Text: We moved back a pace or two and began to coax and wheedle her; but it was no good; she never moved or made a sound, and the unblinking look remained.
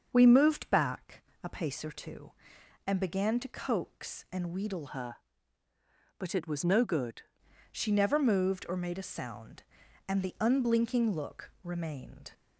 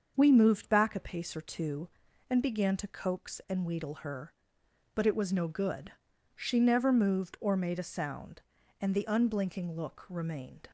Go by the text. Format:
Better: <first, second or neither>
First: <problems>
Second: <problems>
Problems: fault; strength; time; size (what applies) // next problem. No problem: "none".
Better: second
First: starts louder than the rest; until 1.1 s; 6.5 dB // pauses between "back" and "a"; slight; at 1.2 s; 0.20 s long // changes voice from "her" to "good"; from 4.8 to 7.2 s; 2.4 s long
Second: starts louder than the rest; until 1.1 s; 6.5 dB